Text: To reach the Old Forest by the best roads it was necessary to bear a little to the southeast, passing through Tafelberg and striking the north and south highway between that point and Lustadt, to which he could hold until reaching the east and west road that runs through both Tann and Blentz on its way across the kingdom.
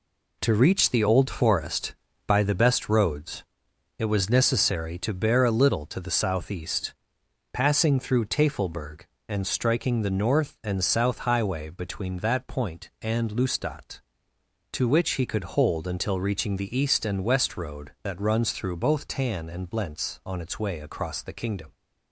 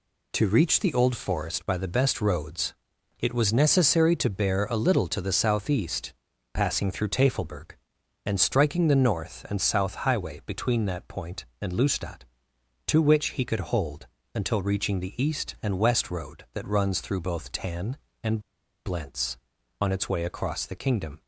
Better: first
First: pauses between "roads" and "it"; noticeable; at 3.4 s; 0.56 s long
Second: pauses between "roads" and "it"; noticeable; at 2.7 s; 0.46 s long // pauses between "hold" and "until"; slight; at 14.0 s; 0.26 s long // pauses between "and" and "Blentz"; noticeable; at 18.3 s; 0.46 s long

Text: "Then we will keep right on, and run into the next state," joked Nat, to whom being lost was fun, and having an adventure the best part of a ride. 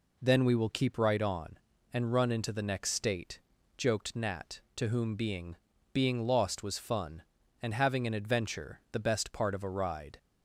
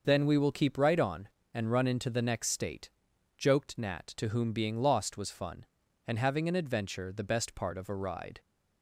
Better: second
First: says "being" twice; at 5.9 s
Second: none

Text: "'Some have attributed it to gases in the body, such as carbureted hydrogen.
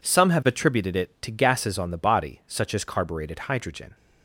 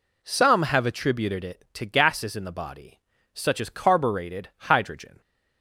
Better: second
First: says "on" for "in"; at 1.7 s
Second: none

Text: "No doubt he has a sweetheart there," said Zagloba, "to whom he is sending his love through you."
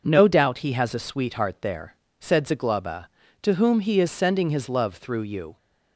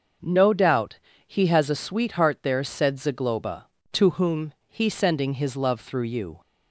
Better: first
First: none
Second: starts louder than the rest; noticeable; until 1.5 s; 6 dB // pauses between "doubt" and "he"; slight; at 0.9 s; 0.30 s long // pauses between "whom" and "he"; slight; at 4.5 s; 0.16 s long // skips "is"; at 4.8 s

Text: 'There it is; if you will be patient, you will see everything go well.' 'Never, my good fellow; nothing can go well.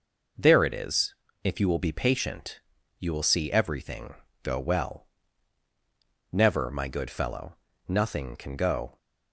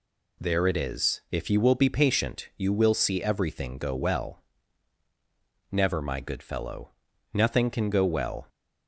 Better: second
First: pauses between "everything" and "go"; slight; at 4.1 s; 0.28 s long // stops before "well"; at 8.9 s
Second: none

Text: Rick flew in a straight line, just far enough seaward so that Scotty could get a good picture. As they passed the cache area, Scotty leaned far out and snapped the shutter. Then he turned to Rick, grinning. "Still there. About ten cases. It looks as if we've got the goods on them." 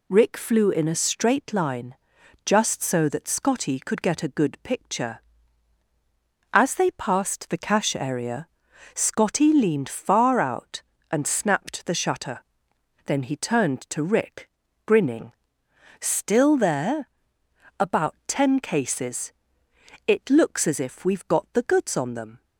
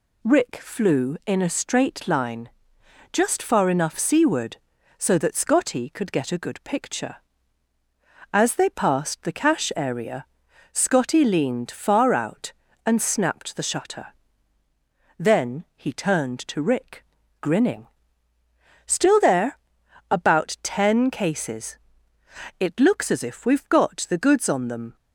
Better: second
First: skips "far enough seaward"; at 2.8 s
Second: none

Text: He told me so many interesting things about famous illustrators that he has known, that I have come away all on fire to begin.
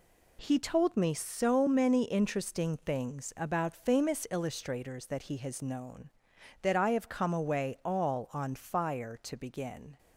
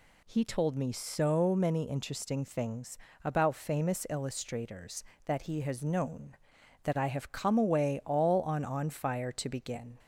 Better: first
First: none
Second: pauses between "things" and "about"; slight; at 2.9 s; 0.28 s long // says "on" twice; at 8.6 s

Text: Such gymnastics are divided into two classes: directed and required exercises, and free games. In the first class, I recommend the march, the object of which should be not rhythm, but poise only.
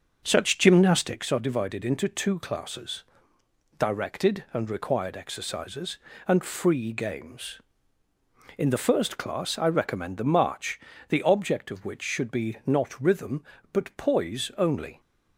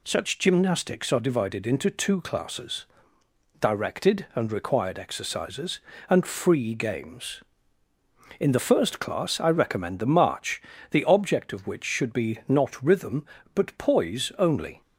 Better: second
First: starts louder than the rest; until 1.2 s; 6.5 dB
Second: none

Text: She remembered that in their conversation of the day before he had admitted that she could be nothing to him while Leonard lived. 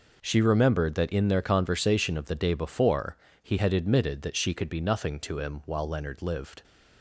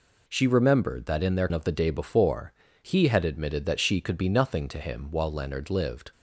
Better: first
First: pauses between "before" and "he"; slight; at 3.1 s; 0.26 s long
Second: skips "conversation"; at 1.5 s // pauses between "before" and "he"; slight; at 2.5 s; 0.30 s long

